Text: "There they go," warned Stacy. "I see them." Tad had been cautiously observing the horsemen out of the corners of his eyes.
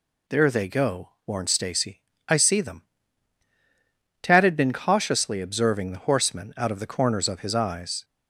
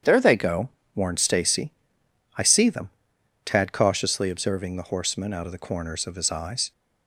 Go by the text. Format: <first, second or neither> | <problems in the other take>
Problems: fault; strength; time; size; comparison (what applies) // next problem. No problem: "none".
first | starts louder than the rest; strong; until 1.3 s; 8.5 dB // skips "had been"; at 3.7 s